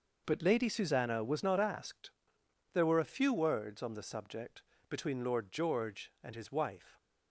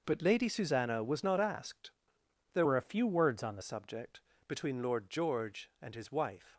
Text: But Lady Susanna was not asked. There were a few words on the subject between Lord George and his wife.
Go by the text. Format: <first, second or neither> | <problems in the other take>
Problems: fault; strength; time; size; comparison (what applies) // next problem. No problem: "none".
first | changes voice from "were" to "the"; from 2.6 to 3.6 s; 1.0 s long // pauses between "subject" and "between"; slight; at 4.2 s; 0.26 s long; slight in the first